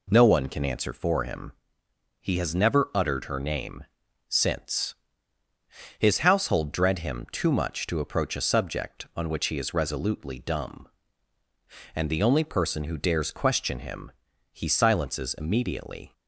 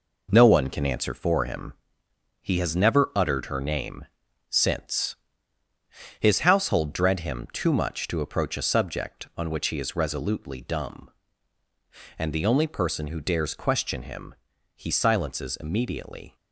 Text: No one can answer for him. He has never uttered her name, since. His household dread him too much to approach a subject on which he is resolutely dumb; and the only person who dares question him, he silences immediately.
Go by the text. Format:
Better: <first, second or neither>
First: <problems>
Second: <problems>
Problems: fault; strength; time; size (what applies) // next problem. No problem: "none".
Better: first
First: none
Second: gets quieter; throughout; 6.5 dB